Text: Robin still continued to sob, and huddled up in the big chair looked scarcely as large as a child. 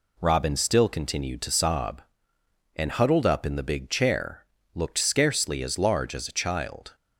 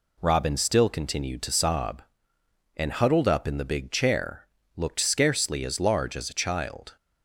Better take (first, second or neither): neither